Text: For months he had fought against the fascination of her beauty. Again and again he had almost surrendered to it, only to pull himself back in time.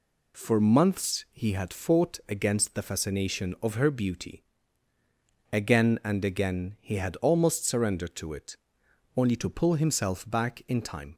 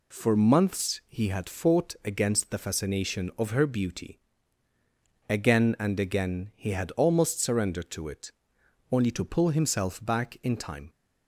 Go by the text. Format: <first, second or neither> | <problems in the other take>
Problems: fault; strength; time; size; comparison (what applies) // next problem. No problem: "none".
neither | none